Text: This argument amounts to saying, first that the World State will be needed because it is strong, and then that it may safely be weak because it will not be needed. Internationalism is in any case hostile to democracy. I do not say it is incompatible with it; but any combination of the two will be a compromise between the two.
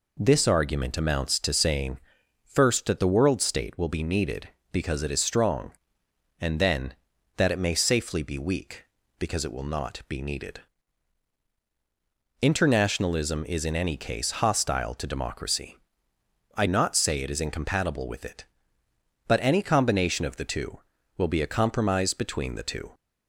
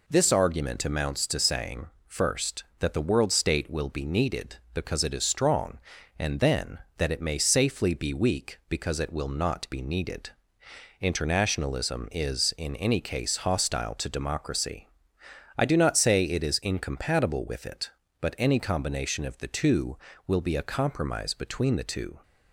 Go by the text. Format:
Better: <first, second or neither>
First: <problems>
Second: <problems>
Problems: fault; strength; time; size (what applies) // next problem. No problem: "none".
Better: second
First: skips "do"; at 16.6 s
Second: none